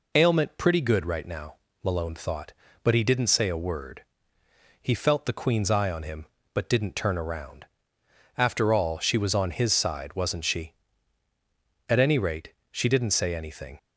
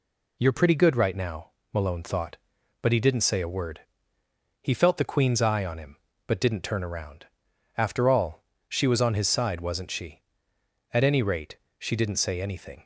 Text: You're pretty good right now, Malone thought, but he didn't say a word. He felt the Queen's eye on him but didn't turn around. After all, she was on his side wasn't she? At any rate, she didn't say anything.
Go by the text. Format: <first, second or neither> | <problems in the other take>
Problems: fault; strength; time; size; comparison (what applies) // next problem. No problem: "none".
second | says "Ailment" for "You're"; at 0.1 s